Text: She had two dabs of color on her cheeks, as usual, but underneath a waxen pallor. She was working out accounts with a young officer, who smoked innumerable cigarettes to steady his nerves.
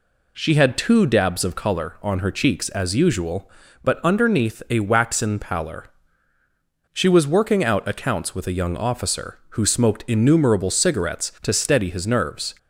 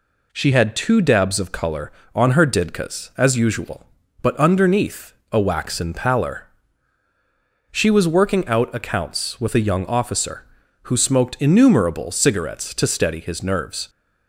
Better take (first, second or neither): first